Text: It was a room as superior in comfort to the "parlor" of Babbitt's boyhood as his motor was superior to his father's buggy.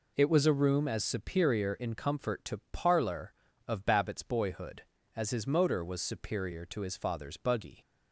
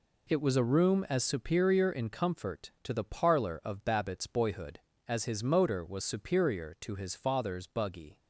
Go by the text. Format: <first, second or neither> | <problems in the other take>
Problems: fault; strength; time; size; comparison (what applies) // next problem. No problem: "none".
second | skips "the"; at 2.6 s